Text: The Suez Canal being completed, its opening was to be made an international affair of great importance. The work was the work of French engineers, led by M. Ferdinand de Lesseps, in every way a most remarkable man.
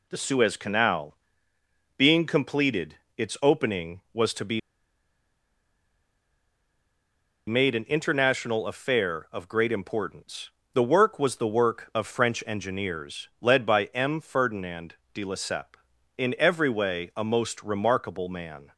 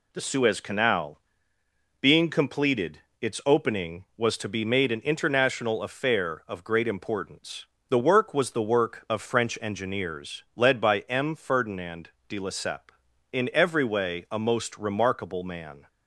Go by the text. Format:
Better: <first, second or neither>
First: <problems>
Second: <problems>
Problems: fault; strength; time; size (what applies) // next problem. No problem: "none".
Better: second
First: pauses between "Canal" and "being"; noticeable; at 1.1 s; 0.82 s long // pauses between "be" and "made"; strong; at 4.5 s; 2.8 s long // pauses between "Ferdinand" and "de"; slight; at 14.9 s; 0.22 s long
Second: pauses between "Canal" and "being"; noticeable; at 1.1 s; 0.82 s long // pauses between "Ferdinand" and "de"; slight; at 12.0 s; 0.22 s long